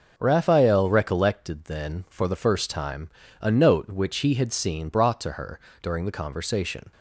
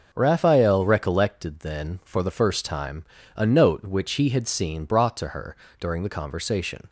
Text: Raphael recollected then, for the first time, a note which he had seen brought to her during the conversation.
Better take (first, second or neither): neither